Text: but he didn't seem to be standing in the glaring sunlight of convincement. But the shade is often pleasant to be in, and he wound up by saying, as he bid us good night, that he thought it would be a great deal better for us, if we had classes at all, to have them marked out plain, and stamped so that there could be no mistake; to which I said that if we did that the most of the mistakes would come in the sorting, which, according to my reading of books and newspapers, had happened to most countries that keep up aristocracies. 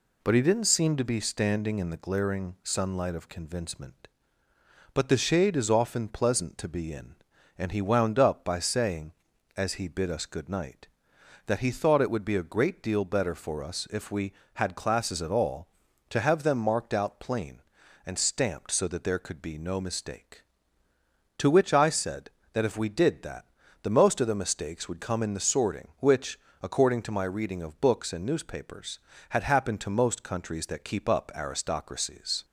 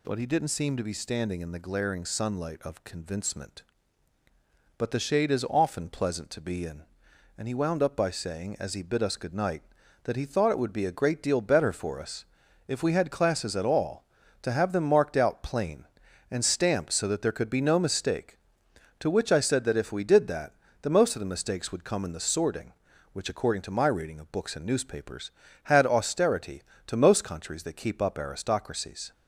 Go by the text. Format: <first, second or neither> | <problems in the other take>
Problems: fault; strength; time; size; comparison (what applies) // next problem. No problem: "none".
first | pauses between "that" and "the"; slight; at 20.5 s; 0.30 s long; also in the first // says "austerity" for "happened"; at 25.8 s